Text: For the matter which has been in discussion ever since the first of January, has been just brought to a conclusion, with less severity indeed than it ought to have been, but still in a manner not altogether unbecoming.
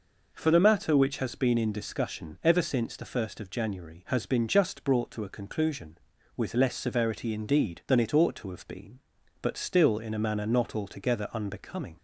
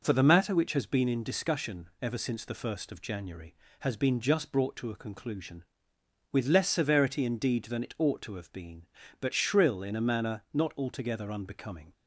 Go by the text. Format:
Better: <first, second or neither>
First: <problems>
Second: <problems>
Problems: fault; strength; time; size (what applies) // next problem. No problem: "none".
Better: first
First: none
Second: says "shrill" for "still"; at 9.3 s